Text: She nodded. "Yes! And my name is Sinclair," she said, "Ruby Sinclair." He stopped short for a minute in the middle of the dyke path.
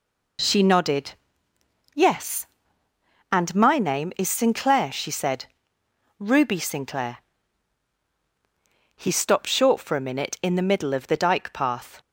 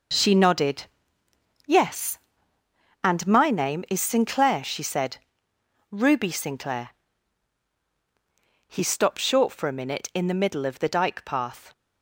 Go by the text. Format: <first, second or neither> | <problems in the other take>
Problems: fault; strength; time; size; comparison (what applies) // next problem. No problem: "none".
first | gets quieter; strong; throughout; 8.5 dB